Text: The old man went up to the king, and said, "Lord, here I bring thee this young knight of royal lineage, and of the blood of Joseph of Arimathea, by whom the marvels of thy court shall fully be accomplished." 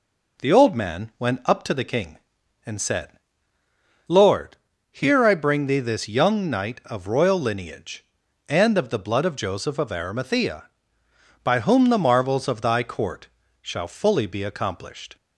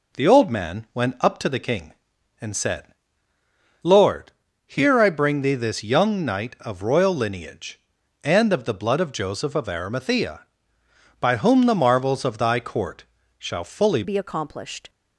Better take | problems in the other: first | pauses between "court" and "shall"; slight; at 13.0 s; 0.34 s long; slight in the first // changes voice at "be"; from 14.0 s on; 0.8 s long

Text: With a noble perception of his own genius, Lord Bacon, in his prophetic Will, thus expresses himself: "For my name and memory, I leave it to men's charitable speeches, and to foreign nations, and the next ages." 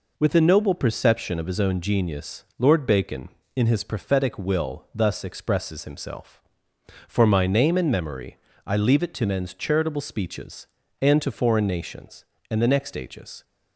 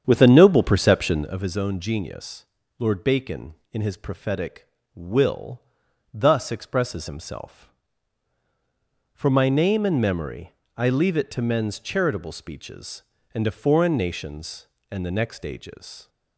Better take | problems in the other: first | starts louder than the rest; strong; until 1.5 s; 8 dB

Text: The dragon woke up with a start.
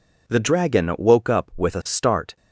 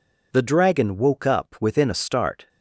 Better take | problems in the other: first | says "within" for "with"; at 1.5 s

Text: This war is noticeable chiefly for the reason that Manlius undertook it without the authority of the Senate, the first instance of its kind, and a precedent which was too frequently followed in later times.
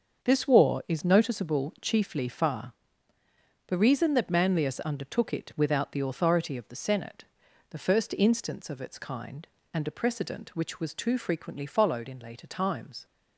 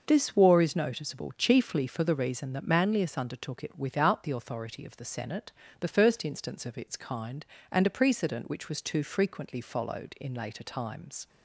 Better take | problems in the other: second | starts louder than the rest; until 1.2 s; 6.5 dB // says "far" for "for"; at 2.2 s

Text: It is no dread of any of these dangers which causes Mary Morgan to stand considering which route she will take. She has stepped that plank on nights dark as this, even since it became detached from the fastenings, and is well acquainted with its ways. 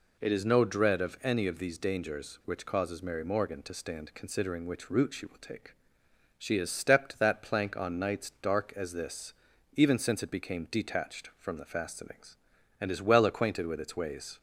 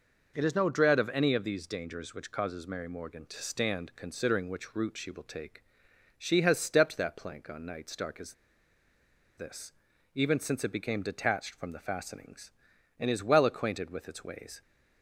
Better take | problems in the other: first | pauses between "as" and "this"; at 8.3 s; 1.0 s long

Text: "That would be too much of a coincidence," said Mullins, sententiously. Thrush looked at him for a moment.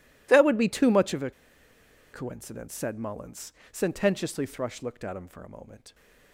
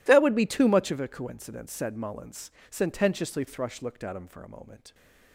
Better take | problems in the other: second | pauses between "a" and "coincidence"; noticeable; at 1.3 s; 0.81 s long

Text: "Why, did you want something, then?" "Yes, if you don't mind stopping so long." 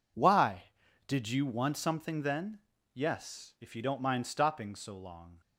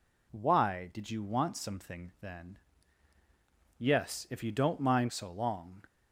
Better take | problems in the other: first | skips "stopping"; at 5.1 s

